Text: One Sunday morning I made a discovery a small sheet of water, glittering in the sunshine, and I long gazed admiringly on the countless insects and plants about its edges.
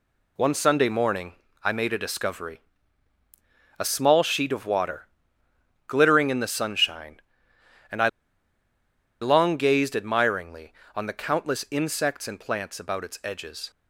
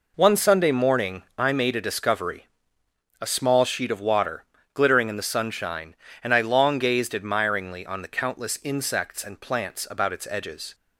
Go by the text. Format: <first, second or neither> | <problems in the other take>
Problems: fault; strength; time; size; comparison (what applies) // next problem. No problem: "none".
second | pauses between "morning" and "I"; slight; at 1.3 s; 0.32 s long // pauses between "discovery" and "a"; at 2.6 s; 1.1 s long; noticeable in the second // pauses between "I" and "long"; at 8.0 s; 1.1 s long